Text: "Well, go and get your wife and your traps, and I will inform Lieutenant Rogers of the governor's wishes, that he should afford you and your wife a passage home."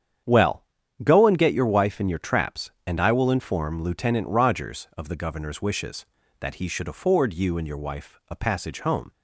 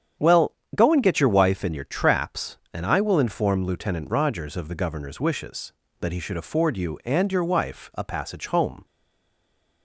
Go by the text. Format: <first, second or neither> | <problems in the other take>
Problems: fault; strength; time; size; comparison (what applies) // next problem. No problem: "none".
first | starts louder than the rest; strong; until 1.4 s; 8.5 dB; strong in the first // stays silent after the last word; from 8.8 s on; 1.0 s long